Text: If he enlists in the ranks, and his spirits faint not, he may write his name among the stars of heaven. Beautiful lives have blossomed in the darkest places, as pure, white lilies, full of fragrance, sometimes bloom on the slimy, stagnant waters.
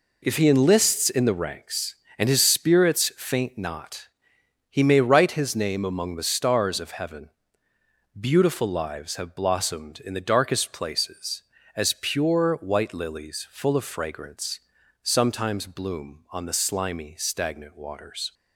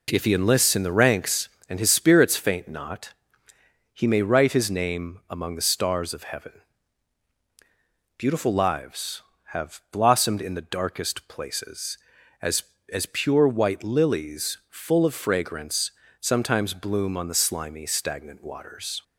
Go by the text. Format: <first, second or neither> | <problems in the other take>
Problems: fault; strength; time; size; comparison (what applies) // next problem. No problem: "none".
first | says "as" twice; at 12.9 s